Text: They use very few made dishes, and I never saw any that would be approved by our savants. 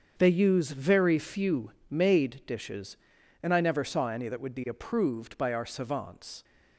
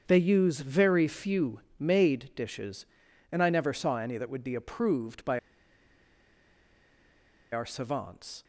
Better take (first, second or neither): first